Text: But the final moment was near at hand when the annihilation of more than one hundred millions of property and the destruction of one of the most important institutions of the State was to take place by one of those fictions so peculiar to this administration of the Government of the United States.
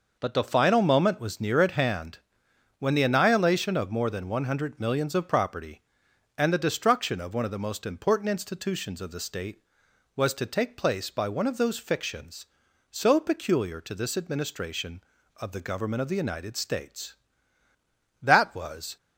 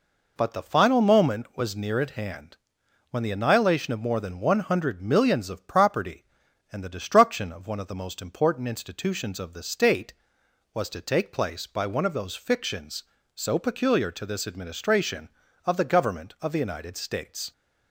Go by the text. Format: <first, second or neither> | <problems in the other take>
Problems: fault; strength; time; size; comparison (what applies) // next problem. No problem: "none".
second | pauses between "hand" and "when"; noticeable; at 2.1 s; 0.62 s long; noticeable in the second // goes on to say "That was"; noticeable; from 18.2 s on; 0.74 s long